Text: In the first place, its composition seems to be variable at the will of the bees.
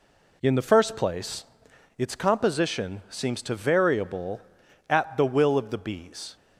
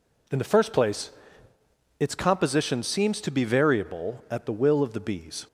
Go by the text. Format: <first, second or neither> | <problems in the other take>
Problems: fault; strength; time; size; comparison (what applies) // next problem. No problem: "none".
second | skips "be"; at 3.5 s